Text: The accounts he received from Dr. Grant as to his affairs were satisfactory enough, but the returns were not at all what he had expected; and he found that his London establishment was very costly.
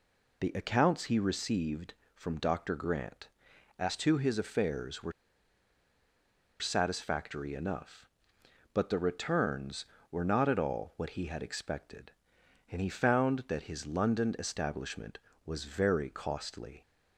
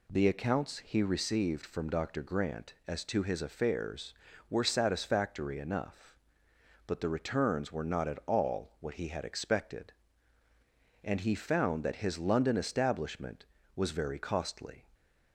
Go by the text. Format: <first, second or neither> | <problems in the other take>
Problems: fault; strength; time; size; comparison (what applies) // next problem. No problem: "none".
second | pauses between "were" and "satisfactory"; strong; at 5.1 s; 1.4 s long